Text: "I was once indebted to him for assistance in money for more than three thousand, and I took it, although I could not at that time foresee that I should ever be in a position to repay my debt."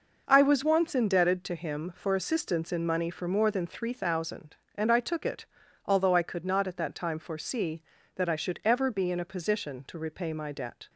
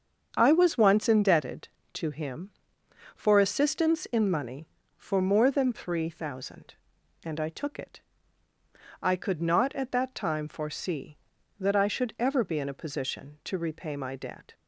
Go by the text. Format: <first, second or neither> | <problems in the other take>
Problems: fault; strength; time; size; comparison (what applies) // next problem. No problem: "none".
first | starts louder than the rest; strong; until 1.3 s; 7.5 dB // skips "although"; at 8.5 s